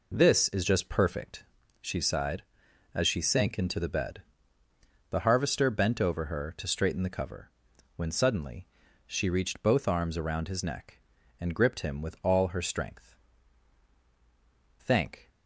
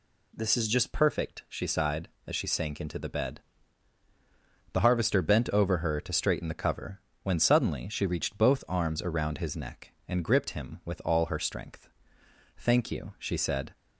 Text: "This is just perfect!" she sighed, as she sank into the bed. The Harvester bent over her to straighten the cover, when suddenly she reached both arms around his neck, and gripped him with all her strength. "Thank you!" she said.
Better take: second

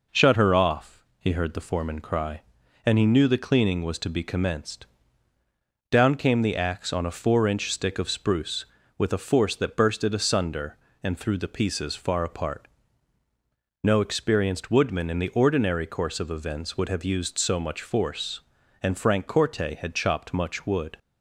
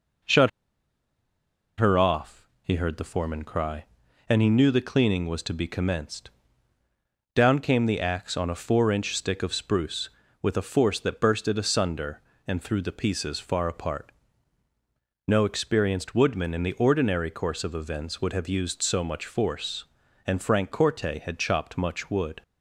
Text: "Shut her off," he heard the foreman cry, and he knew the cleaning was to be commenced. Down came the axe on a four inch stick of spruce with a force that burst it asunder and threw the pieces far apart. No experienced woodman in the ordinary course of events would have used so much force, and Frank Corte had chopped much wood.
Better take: first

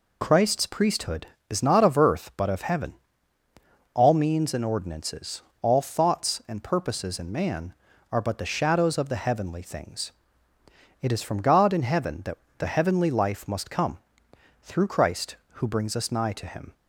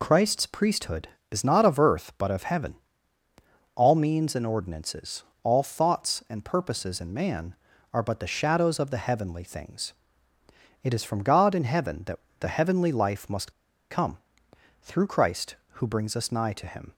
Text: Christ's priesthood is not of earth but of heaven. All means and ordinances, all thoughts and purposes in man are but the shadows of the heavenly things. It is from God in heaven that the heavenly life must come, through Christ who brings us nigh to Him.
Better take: first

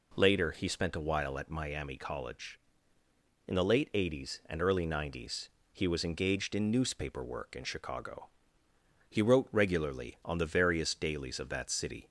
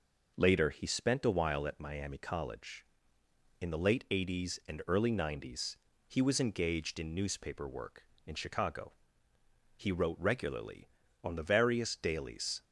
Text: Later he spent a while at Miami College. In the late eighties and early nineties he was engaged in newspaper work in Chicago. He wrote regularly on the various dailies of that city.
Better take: first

